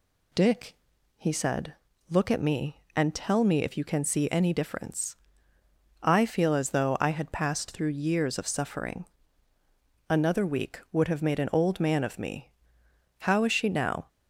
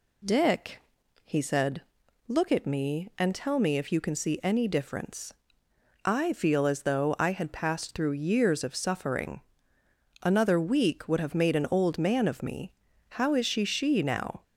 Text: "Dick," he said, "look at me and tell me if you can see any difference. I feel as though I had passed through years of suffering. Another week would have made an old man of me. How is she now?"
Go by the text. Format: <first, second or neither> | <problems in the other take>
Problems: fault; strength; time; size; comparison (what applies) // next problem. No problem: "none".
first | says "she" twice; at 13.6 s